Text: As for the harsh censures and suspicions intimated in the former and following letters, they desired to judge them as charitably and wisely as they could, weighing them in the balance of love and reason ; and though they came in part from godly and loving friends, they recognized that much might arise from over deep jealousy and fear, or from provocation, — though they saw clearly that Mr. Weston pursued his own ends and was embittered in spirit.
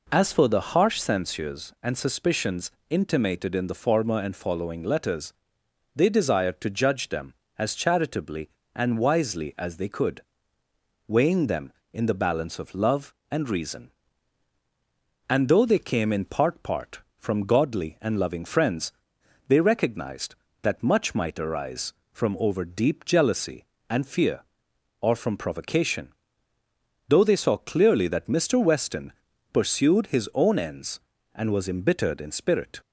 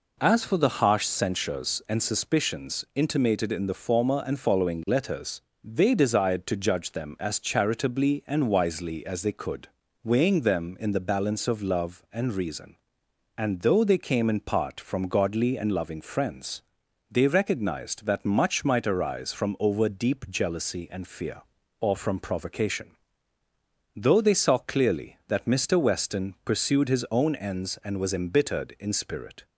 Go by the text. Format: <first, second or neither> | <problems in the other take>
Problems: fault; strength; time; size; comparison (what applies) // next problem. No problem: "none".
second | pauses between "suspicions" and "intimated"; slight; at 2.7 s; 0.16 s long // says "part" twice; at 16.6 s // pauses between "Weston" and "pursued"; at 29.1 s; 0.42 s long